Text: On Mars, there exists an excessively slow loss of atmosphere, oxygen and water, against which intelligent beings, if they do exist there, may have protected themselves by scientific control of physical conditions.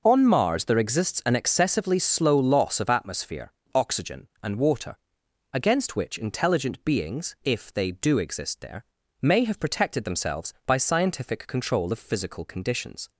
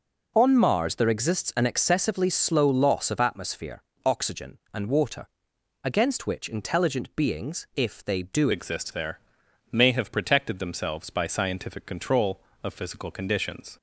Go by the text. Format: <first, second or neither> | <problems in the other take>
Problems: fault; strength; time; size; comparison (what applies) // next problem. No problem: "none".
first | changes voice at "exist"; from 8.5 s on; 5.2 s long